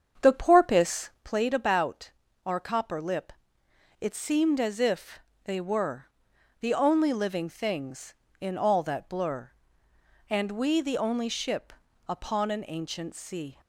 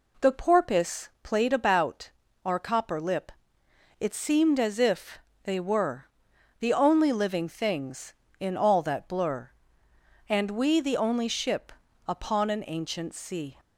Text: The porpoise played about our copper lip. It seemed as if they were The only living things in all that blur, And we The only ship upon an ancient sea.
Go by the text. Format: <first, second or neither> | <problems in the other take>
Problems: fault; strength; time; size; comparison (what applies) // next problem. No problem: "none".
second | starts louder than the rest; strong; until 1.3 s; 7.5 dB // pauses between "about" and "our"; slight; at 2.1 s; 0.36 s long; slight in the second // pauses between "if" and "they"; slight; at 5.2 s; 0.24 s long; slight in the second // pauses between "were" and "The"; noticeable; at 6.0 s; 0.54 s long; noticeable in the second // pauses between "ship" and "upon"; at 11.7 s; 0.38 s long; also in the second